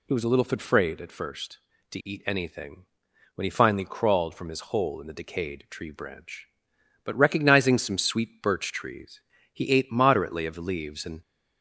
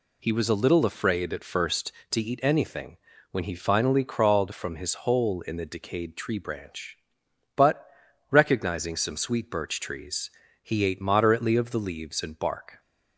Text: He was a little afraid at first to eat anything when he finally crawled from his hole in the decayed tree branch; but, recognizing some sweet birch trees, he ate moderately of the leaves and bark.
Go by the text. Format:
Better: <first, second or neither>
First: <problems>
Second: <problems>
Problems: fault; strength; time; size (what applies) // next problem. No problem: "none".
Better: second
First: pauses between "anything" and "when"; noticeable; at 2.8 s; 0.50 s long // stops before "bark"; at 11.2 s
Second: pauses between "anything" and "when"; slight; at 2.9 s; 0.34 s long